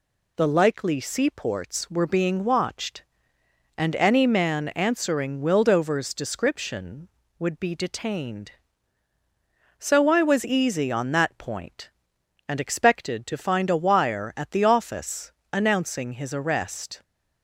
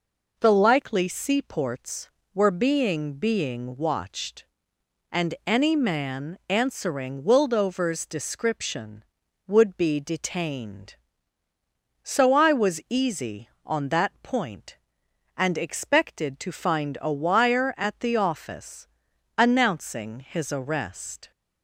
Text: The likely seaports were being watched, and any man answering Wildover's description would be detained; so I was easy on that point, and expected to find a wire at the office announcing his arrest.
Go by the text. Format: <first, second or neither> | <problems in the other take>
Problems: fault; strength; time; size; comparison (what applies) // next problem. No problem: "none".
first | says "being" twice; at 3.1 s // pauses between "office" and "announcing"; noticeable; at 18.8 s; 0.52 s long; slight in the first